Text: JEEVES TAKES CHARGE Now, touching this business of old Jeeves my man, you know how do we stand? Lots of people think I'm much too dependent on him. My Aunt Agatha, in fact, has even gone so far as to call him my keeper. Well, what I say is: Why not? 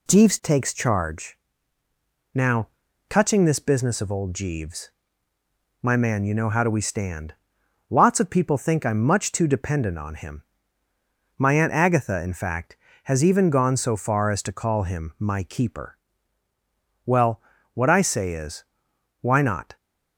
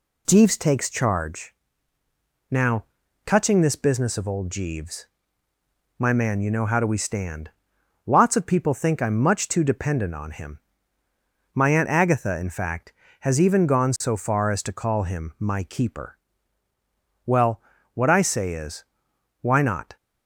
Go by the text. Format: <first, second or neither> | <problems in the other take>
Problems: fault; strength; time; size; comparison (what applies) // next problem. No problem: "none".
neither | pauses between "CHARGE" and "Now"; noticeable; the same in both // pauses between "Jeeves" and "my"; noticeable; the same in both